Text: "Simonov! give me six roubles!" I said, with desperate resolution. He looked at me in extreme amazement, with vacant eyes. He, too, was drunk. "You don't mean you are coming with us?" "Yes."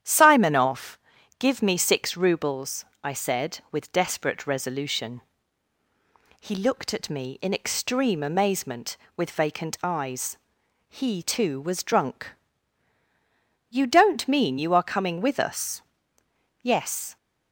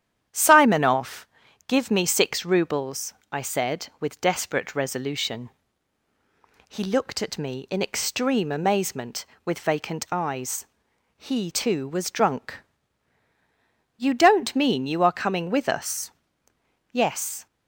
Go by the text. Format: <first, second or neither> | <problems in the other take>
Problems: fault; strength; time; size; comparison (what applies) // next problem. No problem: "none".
neither | starts louder than the rest; strong; the same in both